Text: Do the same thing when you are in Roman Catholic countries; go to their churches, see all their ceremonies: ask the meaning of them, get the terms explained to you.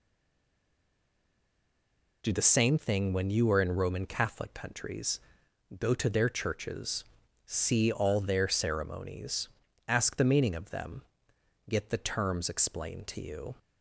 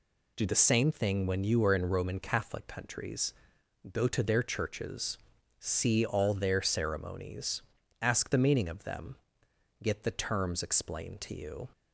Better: second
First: stays silent before the first word; until 2.2 s; 2.2 s long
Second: none

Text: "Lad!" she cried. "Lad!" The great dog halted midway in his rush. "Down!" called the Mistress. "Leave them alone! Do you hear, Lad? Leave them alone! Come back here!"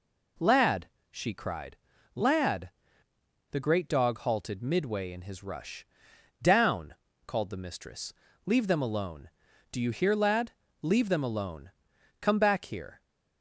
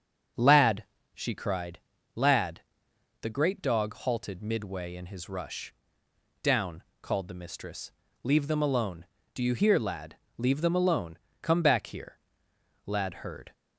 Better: first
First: none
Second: starts louder than the rest; strong; until 1.6 s; 7 dB // goes on to say "Lad heard"; noticeable; from 12.8 s on; 0.68 s long

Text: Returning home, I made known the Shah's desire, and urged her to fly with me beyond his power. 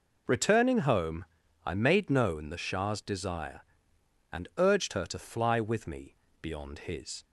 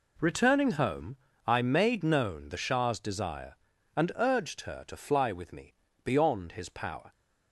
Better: second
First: pauses between "me" and "beyond"; slight; at 6.1 s; 0.24 s long // stops before "power"; at 7.2 s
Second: pauses between "me" and "beyond"; slight; at 5.7 s; 0.32 s long

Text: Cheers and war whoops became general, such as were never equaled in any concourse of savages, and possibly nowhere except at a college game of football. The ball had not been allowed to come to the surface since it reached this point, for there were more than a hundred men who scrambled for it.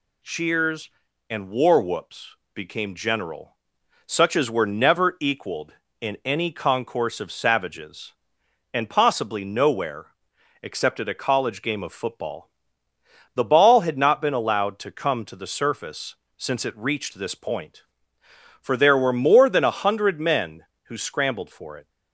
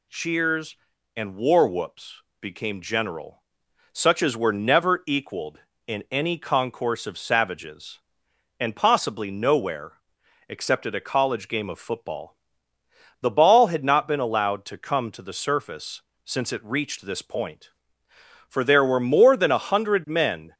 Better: first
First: pauses between "whoops" and "became"; slight; at 2.3 s; 0.20 s long // pauses between "nowhere" and "except"; noticeable; at 10.0 s; 0.58 s long // pauses between "surface" and "since"; slight; at 16.1 s; 0.23 s long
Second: pauses between "whoops" and "became"; slight; at 2.2 s; 0.20 s long // pauses between "nowhere" and "except"; noticeable; at 9.9 s; 0.58 s long // pauses between "surface" and "since"; slight; at 16.0 s; 0.24 s long // stops before "who scrambled for it"; at 20.5 s

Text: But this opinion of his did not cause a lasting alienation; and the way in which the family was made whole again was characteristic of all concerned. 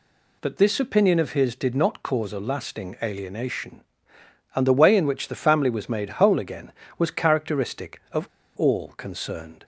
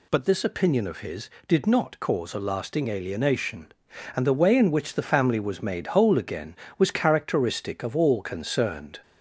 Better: second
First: pauses between "of" and "all"; slight; at 8.2 s; 0.32 s long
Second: none

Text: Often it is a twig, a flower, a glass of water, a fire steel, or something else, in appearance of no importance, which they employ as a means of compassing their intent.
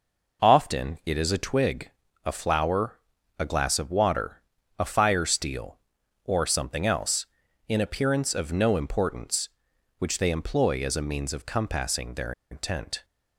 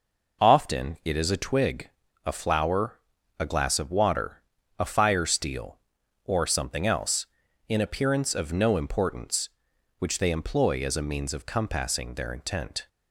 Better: second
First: pauses between "their" and "intent"; slight; at 12.3 s; 0.19 s long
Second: none

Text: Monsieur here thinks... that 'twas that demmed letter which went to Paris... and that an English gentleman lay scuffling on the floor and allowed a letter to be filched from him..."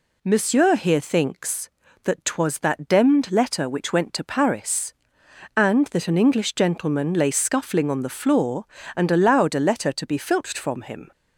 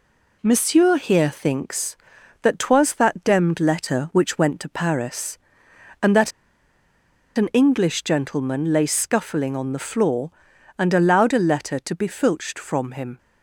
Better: first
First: none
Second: pauses between "that" and "an"; at 6.3 s; 1.0 s long

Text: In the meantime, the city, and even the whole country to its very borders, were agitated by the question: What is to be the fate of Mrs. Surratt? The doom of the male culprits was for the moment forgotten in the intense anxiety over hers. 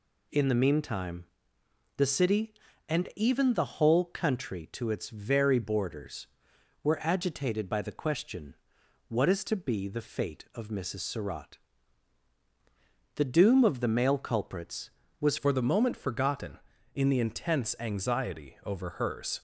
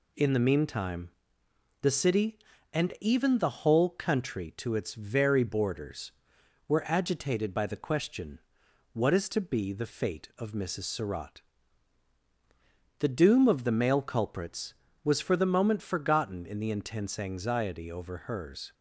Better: second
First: changes voice at "for"; from 15.3 s on; 4.1 s long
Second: none

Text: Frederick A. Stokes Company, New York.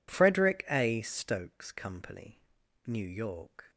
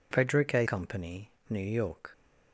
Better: first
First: none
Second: skips "Stokes"; at 0.6 s

